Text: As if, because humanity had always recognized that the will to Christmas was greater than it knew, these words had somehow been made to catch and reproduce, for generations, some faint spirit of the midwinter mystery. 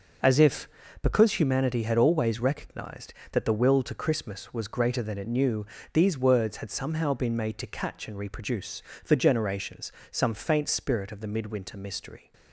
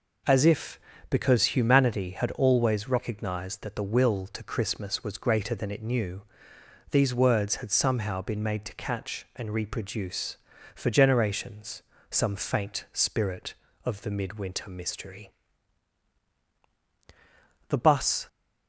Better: first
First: none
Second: goes on to say "The bus"; from 17.6 s on; 0.60 s long

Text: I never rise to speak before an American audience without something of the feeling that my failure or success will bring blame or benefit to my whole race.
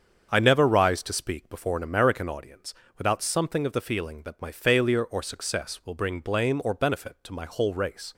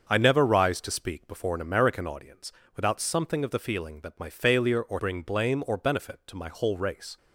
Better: first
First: starts louder than the rest; strong; until 1.3 s; 7 dB // pauses between "audience" and "without"; slight; at 2.7 s; 0.24 s long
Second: starts louder than the rest; until 1.1 s; 6.5 dB // pauses between "audience" and "without"; slight; at 2.5 s; 0.24 s long // skips "success will"; at 4.9 s

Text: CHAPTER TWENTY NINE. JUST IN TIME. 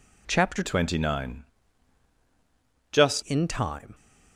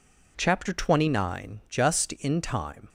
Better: second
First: changes voice from "TWENTY" to "JUST"; from 0.6 to 3.2 s; 2.6 s long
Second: none

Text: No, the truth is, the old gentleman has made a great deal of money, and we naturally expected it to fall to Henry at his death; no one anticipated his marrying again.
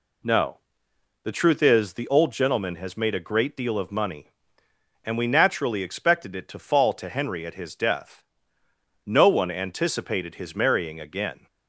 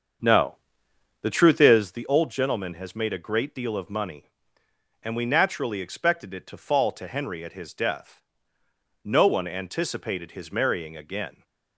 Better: first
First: none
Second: starts louder than the rest; until 1.9 s; 7 dB

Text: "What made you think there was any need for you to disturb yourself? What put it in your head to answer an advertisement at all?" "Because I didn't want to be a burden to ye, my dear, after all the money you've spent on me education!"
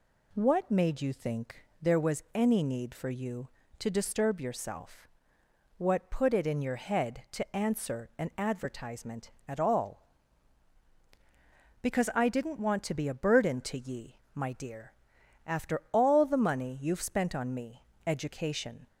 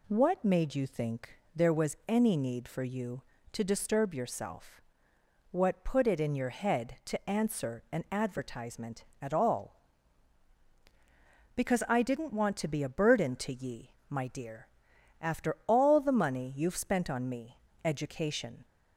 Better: neither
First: pauses between "think" and "there"; slight; at 1.6 s; 0.16 s long // pauses between "me" and "education"; slight; at 17.8 s; 0.24 s long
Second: pauses between "think" and "there"; slight; at 1.3 s; 0.16 s long // pauses between "me" and "education"; slight; at 17.5 s; 0.27 s long

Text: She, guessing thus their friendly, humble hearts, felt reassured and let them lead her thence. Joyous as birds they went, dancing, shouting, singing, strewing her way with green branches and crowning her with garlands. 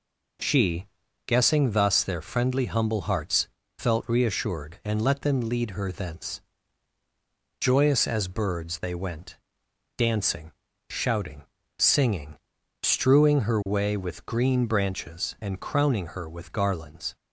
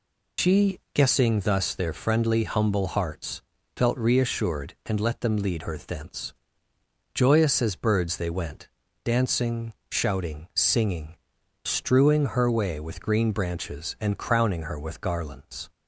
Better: first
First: none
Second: loses the start of "She"; at 0.3 s; 105 ms

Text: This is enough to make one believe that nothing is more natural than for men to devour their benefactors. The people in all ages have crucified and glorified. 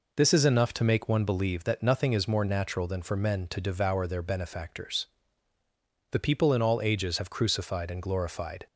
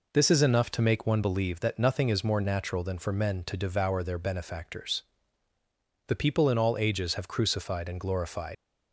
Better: first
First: none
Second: leaves "glorified" unfinished; at 8.5 s; 95 ms

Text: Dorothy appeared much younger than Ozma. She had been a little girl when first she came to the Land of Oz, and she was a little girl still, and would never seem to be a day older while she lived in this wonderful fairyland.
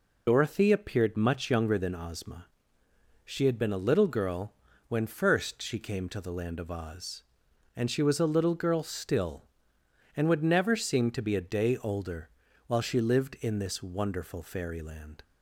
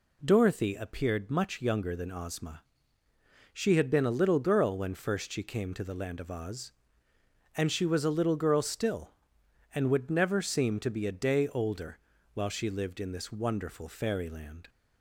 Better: second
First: loses the start of "Dorothy"; at 0.2 s; 40 ms // pauses between "girl" and "when"; slight; at 4.5 s; 0.34 s long // pauses between "older" and "while"; at 12.2 s; 0.38 s long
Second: pauses between "older" and "while"; slight; at 11.9 s; 0.34 s long

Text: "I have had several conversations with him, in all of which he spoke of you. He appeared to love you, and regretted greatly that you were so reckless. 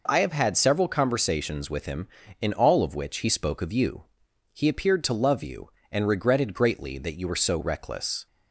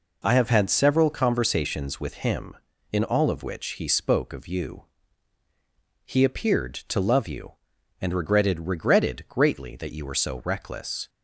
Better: first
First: none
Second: says "regretted" twice; at 8.6 s

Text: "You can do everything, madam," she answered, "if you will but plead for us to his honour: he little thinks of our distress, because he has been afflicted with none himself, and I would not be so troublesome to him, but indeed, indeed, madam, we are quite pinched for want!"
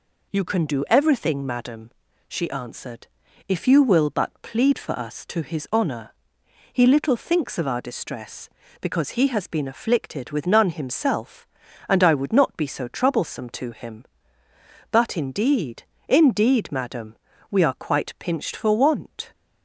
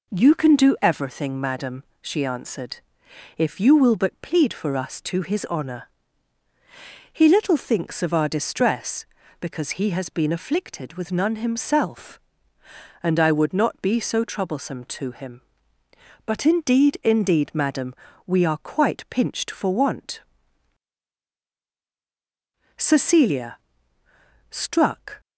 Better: first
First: none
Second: goes on to say "Cecilia struck"; strong; from 22.7 s on; 2.4 s long

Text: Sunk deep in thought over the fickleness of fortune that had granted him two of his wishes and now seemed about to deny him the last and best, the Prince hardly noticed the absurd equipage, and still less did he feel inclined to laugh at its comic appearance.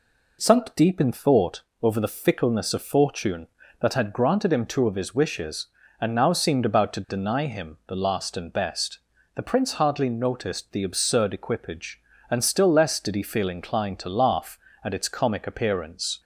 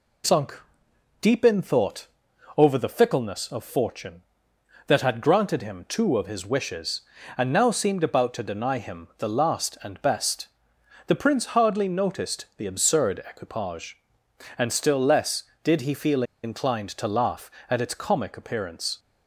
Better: first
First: pauses between "thought" and "over"; slight; at 1.6 s; 0.18 s long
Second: pauses between "Sunk" and "deep"; noticeable; at 0.5 s; 0.62 s long // pauses between "thought" and "over"; noticeable; at 2.0 s; 0.50 s long // pauses between "feel" and "inclined"; slight; at 16.2 s; 0.20 s long

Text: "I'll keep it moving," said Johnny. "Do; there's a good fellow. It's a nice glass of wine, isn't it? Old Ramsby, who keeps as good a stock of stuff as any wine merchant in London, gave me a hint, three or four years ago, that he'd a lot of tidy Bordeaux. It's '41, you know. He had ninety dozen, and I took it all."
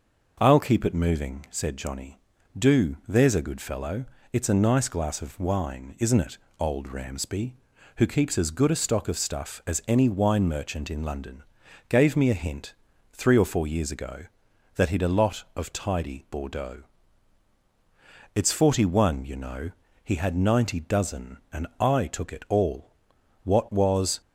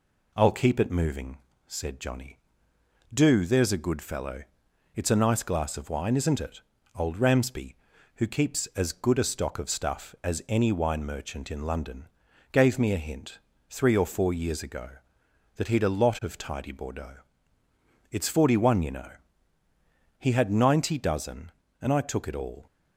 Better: second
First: goes on to say "What was"; noticeable; from 23.4 s on; 0.77 s long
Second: none

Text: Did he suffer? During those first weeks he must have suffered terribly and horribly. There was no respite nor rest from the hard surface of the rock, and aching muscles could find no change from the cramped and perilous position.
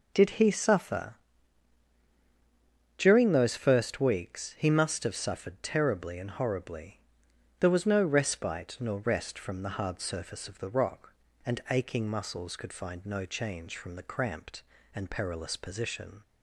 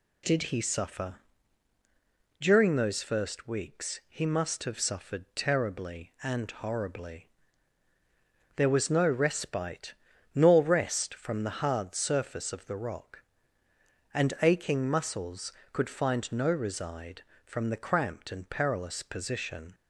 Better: first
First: none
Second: pauses between "respite" and "nor"; at 9.9 s; 0.42 s long // says "reside" for "change"; at 16.4 s

